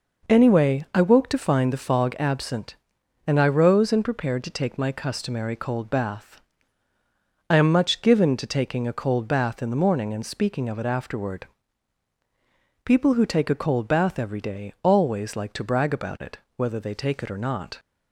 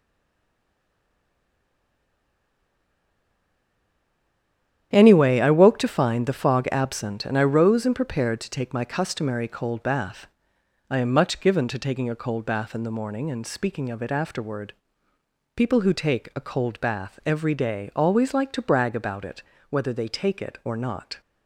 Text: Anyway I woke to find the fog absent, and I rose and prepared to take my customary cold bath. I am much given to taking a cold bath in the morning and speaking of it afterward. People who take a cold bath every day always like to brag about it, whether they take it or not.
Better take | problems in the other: first | stays silent before the first word; strong; until 4.9 s; 4.9 s long // starts louder than the rest; strong; until 5.9 s; 10 dB

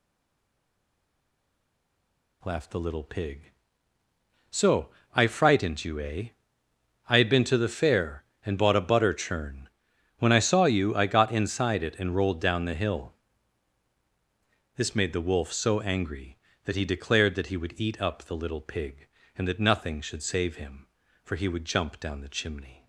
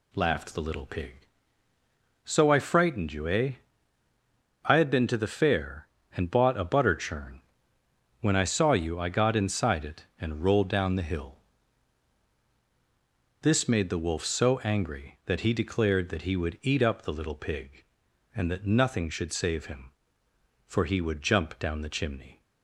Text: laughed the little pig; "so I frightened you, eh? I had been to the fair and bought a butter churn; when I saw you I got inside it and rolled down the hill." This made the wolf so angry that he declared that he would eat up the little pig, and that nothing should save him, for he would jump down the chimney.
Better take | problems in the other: second | stays silent before the first word; until 2.4 s; 2.4 s long // pauses between "so" and "I"; slight; at 4.8 s; 0.26 s long

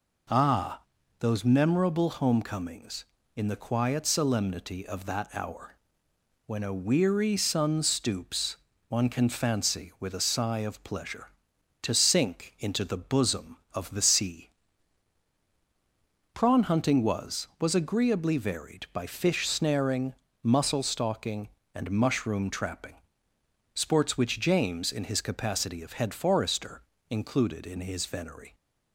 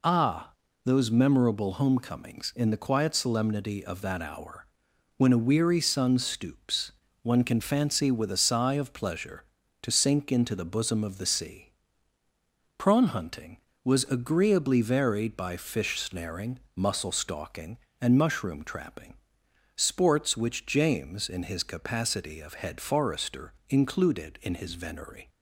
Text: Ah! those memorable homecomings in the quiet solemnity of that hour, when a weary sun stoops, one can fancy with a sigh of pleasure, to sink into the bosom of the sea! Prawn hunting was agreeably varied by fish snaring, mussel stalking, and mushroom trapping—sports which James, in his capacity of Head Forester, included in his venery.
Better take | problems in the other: second | says "was" twice; at 17.5 s

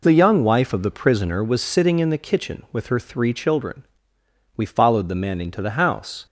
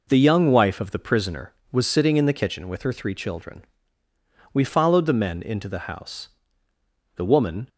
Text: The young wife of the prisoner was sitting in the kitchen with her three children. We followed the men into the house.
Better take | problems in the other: first | goes on to say "The woman"; from 7.1 s on; 0.52 s long

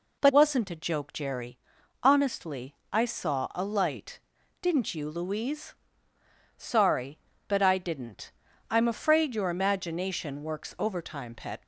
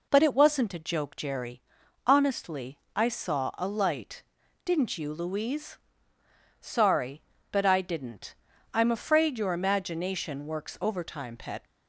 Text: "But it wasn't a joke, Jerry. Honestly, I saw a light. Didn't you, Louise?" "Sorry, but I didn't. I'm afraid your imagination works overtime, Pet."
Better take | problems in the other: second | skips "it"; at 0.3 s

